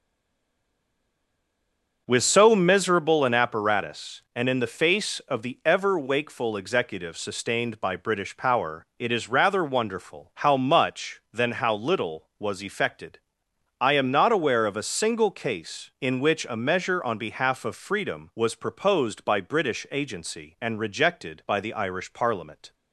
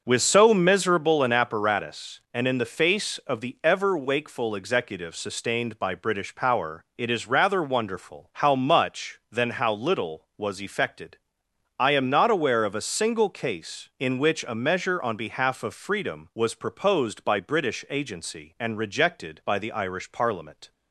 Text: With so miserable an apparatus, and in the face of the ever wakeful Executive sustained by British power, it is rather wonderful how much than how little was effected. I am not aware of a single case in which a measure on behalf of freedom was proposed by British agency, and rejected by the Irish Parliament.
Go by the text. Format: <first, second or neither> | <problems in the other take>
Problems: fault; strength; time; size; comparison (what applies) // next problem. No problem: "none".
second | stays silent before the first word; noticeable; until 2.0 s; 2.0 s long // starts louder than the rest; until 3.0 s; 6.5 dB; also in the second